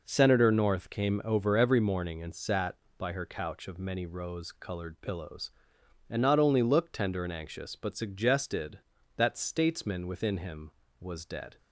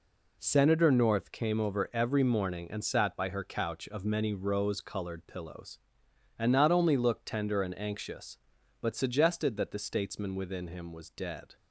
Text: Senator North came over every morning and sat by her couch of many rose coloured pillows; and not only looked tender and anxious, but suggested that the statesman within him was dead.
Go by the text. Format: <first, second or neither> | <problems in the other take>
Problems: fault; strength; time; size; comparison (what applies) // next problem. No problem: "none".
second | skips "the"; at 9.3 s